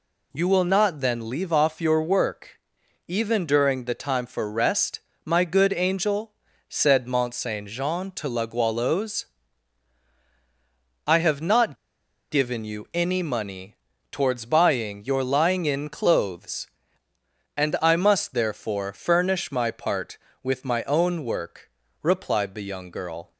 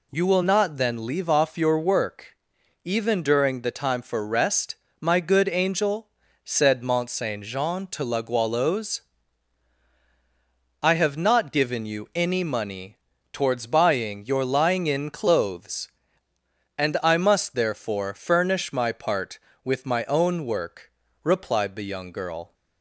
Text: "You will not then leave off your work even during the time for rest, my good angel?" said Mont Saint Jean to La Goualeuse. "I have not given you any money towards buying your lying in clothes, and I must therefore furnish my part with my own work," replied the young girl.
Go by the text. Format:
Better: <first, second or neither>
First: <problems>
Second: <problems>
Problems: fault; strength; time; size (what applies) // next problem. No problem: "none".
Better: second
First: pauses between "work" and "even"; noticeable; at 2.5 s; 0.50 s long // pauses between "not" and "given"; noticeable; at 11.7 s; 0.54 s long // pauses between "money" and "towards"; at 13.7 s; 0.38 s long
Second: pauses between "work" and "even"; noticeable; at 2.3 s; 0.50 s long // pauses between "money" and "towards"; at 12.9 s; 0.38 s long